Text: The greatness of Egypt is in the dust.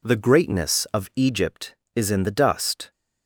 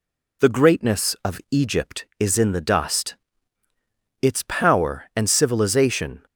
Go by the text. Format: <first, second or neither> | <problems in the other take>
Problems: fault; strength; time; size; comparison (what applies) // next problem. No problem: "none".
first | goes on to say "Its power and civilization"; strong; from 4.2 s on; 2.0 s long